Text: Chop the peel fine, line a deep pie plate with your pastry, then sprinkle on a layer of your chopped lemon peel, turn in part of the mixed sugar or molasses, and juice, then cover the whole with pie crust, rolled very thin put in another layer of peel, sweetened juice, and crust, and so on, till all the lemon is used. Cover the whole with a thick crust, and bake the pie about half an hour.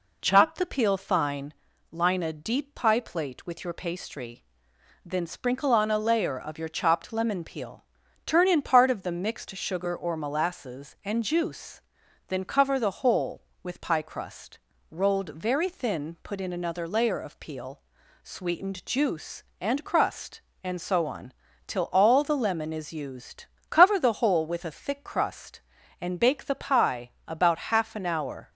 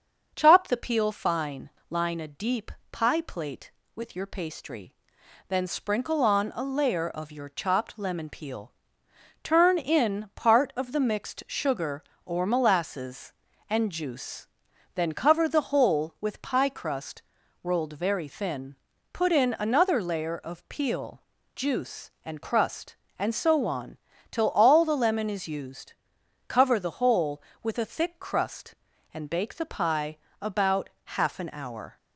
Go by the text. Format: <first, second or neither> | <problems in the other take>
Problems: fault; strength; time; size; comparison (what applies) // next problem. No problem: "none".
first | starts louder than the rest; until 1.3 s; 7 dB // pauses between "deep" and "pie"; slight; at 2.7 s; 0.20 s long // pauses between "thin" and "put"; at 18.7 s; 0.38 s long // skips "sweetened"; at 21.3 s // pauses between "pie" and "about"; slight; at 30.1 s; 0.24 s long; slight in the first